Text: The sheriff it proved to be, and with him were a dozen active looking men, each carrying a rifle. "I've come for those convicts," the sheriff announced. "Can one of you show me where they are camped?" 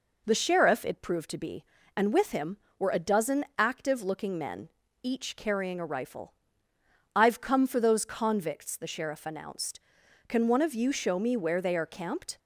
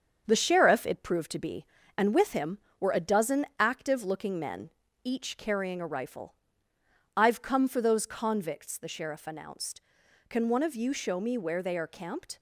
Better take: first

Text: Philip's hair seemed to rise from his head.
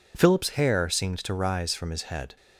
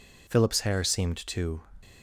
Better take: first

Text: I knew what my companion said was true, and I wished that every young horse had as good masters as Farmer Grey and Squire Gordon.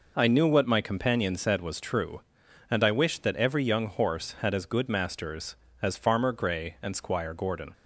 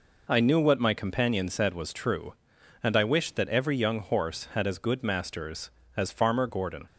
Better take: first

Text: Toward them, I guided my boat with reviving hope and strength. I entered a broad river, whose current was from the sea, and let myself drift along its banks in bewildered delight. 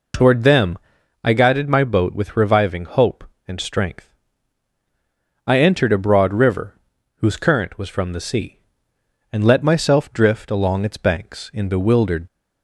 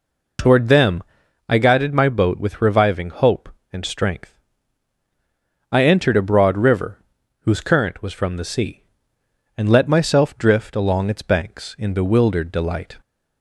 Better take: second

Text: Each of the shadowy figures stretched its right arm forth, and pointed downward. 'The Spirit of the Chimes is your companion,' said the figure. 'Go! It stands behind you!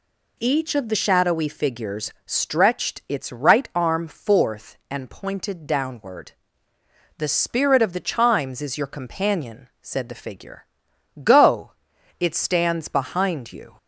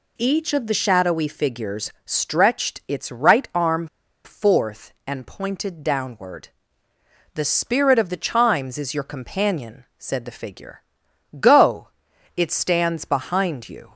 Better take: first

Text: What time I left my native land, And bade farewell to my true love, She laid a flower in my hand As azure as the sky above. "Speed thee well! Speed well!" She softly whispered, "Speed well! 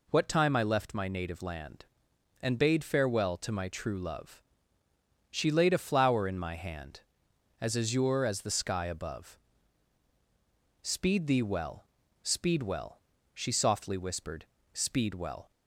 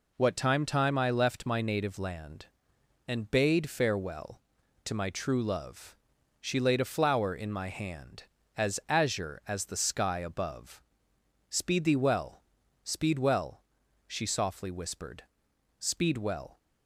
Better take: first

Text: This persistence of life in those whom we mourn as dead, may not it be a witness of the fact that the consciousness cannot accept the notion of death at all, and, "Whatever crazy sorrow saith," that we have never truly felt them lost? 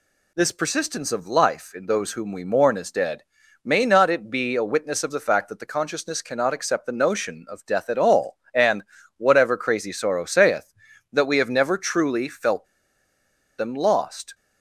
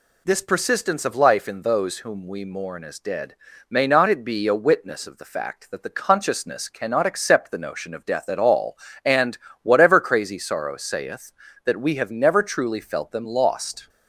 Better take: second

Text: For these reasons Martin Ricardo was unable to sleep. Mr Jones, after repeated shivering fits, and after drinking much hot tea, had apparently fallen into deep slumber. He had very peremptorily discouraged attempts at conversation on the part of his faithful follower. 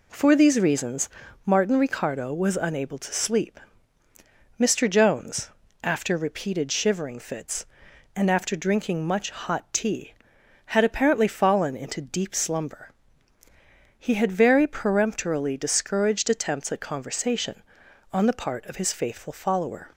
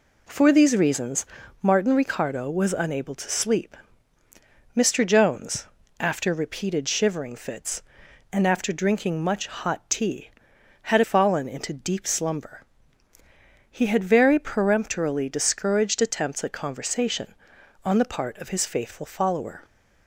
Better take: first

